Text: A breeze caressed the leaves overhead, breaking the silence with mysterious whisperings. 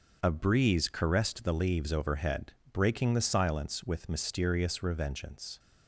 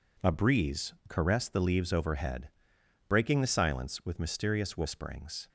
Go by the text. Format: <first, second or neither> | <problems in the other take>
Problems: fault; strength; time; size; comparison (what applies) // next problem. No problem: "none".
second | starts louder than the rest; until 1.2 s; 6.5 dB // says "revengeance" for "whisperings"; at 4.7 s